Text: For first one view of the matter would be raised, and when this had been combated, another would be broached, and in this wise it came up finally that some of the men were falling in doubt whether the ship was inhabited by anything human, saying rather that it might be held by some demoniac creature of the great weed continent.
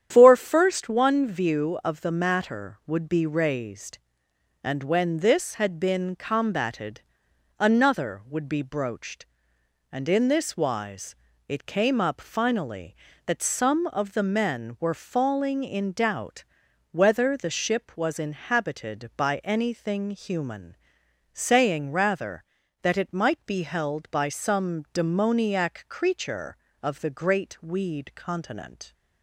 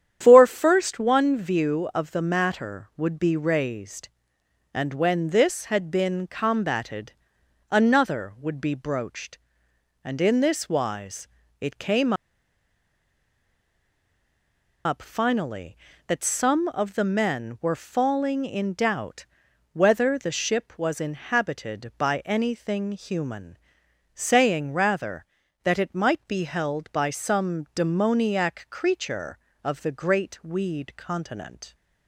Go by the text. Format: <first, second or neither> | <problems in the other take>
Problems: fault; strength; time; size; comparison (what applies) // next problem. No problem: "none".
first | starts louder than the rest; strong; until 1.2 s; 9.5 dB; strong in the first // pauses between "wise" and "it"; slight; at 11.2 s; 0.34 s long; slight in the first // pauses between "came" and "up"; strong; at 12.1 s; 2.7 s long // pauses between "doubt" and "whether"; noticeable; at 19.2 s; 0.46 s long; noticeable in the first